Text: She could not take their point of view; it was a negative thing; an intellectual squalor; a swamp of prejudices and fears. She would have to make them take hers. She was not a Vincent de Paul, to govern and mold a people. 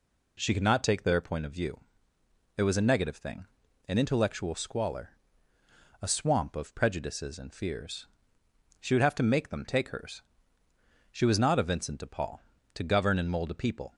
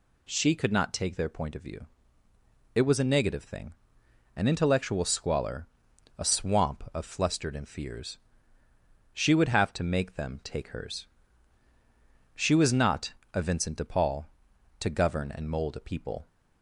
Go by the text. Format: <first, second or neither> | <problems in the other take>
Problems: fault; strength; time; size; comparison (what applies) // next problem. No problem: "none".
first | says "flustered" for "prejudices"; at 7.0 s // pauses between "not" and "a"; slight; at 13.1 s; 0.20 s long